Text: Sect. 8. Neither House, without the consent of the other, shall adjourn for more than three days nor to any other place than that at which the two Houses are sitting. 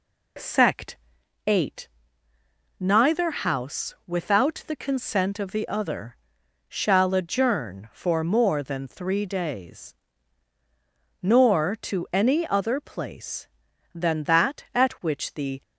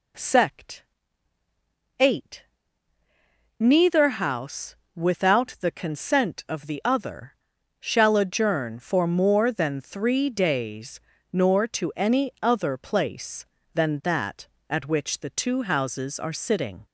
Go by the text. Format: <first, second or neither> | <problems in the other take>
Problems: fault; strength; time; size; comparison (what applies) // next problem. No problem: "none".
second | pauses between "days" and "nor"; strong; at 9.9 s; 1.2 s long; slight in the second // stops before "two Houses are sitting"; at 15.6 s